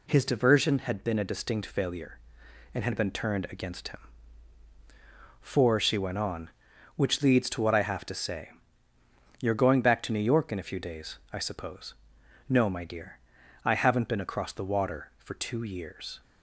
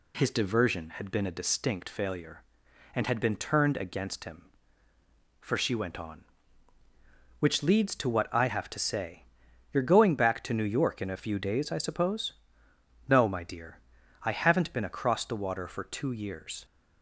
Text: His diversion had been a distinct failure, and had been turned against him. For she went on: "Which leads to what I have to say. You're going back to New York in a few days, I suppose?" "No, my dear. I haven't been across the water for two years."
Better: neither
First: none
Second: none

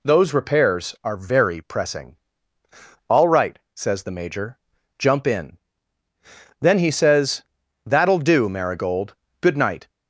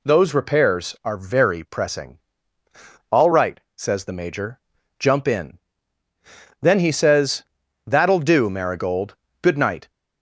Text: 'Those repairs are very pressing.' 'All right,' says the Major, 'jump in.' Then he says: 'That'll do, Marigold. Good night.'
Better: neither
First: none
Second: none

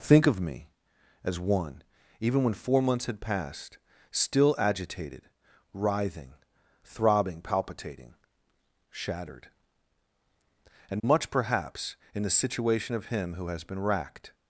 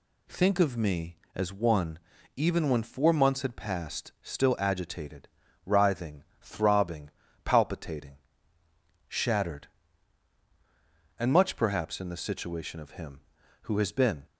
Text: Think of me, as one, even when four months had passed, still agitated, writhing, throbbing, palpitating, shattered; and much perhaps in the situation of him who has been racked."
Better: first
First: none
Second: stops before "racked"; at 14.2 s

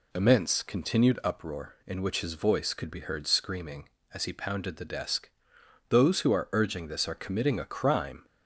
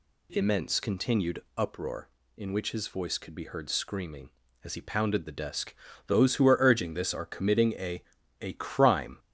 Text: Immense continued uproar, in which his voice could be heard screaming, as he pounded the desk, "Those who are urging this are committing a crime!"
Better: first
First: none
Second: pauses between "continued" and "uproar"; slight; at 1.4 s; 0.16 s long // says "a" twice; at 8.4 s

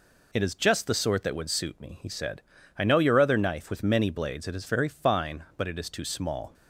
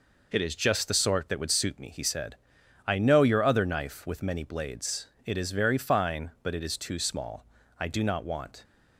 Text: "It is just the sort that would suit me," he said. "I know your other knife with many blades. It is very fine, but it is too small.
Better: first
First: none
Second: goes on to say "I do not want"; noticeable; from 7.7 s on; 0.86 s long

